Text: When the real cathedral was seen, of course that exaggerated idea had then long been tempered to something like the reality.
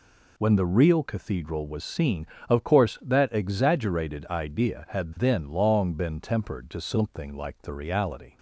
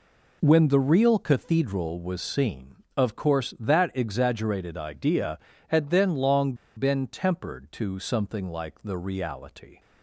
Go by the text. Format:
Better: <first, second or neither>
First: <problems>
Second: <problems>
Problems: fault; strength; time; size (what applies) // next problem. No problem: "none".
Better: first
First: none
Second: pauses between "long" and "been"; slight; at 6.5 s; 0.22 s long